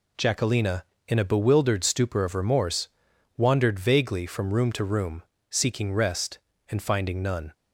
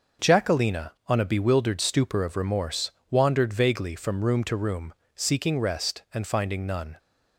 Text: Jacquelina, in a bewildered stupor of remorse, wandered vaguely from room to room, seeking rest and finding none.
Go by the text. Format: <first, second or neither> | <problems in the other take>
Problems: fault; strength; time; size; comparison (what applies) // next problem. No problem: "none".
first | says "on" for "in"; at 1.0 s